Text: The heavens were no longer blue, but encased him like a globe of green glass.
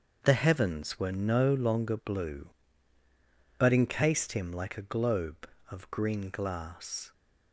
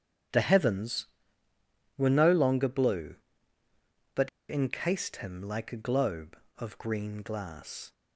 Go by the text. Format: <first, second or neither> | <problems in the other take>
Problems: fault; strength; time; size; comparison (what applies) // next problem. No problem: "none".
first | starts louder than the rest; strong; until 2.2 s; 9 dB; also in the first // pauses between "but" and "encased"; slight; at 4.2 s; 0.20 s long